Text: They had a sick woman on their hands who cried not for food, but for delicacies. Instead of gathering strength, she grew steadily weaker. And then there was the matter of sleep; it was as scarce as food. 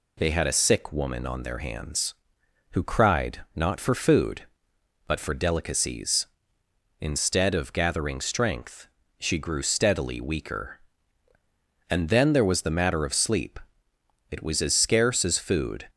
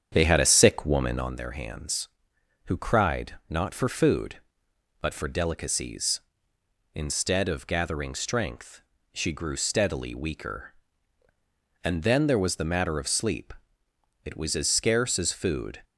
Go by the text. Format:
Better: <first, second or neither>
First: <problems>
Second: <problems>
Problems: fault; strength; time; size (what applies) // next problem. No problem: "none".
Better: first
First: none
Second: starts louder than the rest; strong; until 1.4 s; 8 dB